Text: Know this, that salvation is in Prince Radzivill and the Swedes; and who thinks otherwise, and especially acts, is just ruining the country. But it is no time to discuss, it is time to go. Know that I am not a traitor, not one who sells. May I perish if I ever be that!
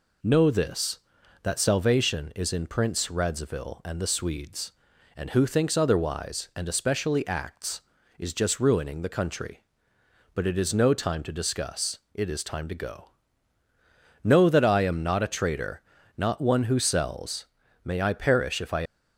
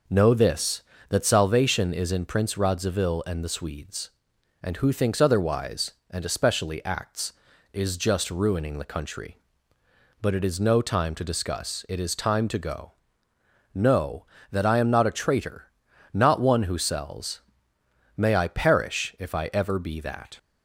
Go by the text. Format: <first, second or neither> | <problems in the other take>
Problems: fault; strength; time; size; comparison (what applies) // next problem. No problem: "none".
second | stops before "ever be that"; at 18.8 s